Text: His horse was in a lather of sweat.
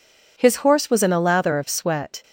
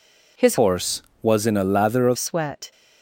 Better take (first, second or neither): first